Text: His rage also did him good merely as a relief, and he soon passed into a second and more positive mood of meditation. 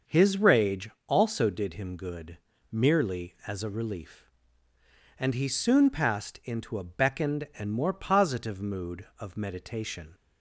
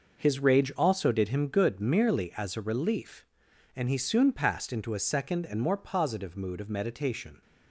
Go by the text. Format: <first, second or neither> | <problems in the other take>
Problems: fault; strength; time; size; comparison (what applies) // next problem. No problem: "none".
second | starts louder than the rest; until 1.2 s; 6.5 dB // pauses between "rage" and "also"; slight; at 0.8 s; 0.20 s long // pauses between "good" and "merely"; slight; at 2.3 s; 0.32 s long // says "beckoned" for "second"; at 6.8 s